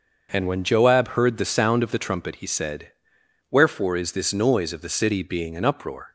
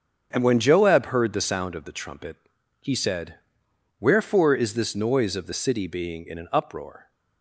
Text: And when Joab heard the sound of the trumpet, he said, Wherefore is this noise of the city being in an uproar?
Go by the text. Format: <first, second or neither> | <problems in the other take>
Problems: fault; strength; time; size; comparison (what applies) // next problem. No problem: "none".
second | starts louder than the rest; until 1.3 s; 6.5 dB; strong in the second // skips "in"; at 5.5 s